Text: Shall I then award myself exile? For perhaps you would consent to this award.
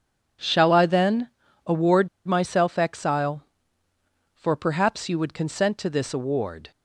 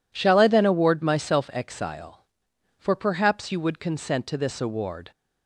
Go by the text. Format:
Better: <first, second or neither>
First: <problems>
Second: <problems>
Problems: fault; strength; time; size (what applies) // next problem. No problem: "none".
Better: second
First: pauses between "then" and "award"; at 1.2 s; 0.38 s long // pauses between "award" and "myself"; slight; at 2.0 s; 0.18 s long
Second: none